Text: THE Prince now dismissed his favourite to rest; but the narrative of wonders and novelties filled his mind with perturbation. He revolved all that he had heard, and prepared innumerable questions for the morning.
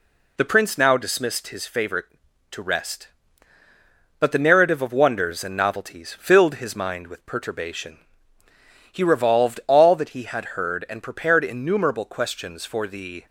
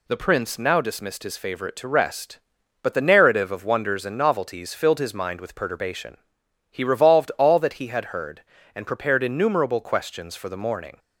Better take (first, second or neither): second